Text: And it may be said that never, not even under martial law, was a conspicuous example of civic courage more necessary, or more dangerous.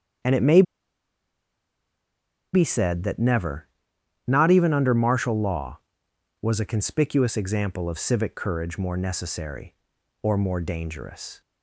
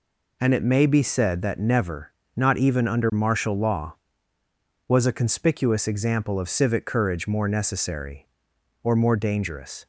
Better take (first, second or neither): second